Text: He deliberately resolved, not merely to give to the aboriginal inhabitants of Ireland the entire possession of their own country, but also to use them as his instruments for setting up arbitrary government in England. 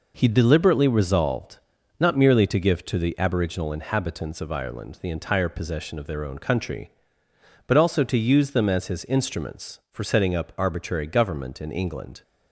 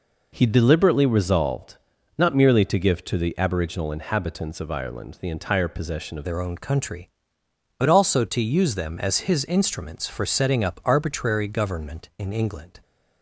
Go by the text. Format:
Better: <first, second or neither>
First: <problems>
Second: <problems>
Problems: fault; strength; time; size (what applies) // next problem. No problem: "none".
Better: first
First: none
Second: changes voice at "their"; from 6.2 s on; 6.5 s long